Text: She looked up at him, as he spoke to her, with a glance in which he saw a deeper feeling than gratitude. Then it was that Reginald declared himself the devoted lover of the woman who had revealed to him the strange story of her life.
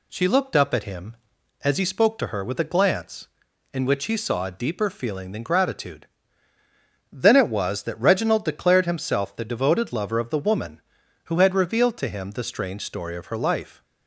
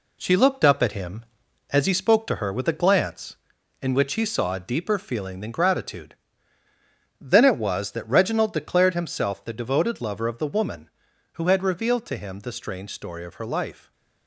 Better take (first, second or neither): first